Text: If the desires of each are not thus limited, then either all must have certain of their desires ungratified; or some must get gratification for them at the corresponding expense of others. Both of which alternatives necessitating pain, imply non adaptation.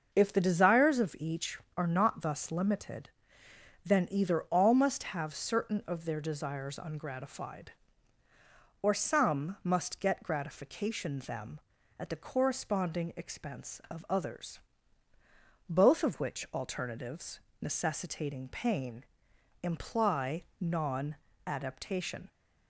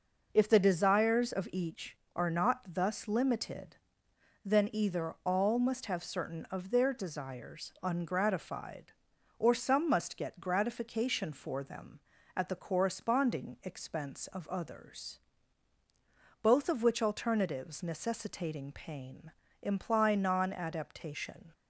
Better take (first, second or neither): second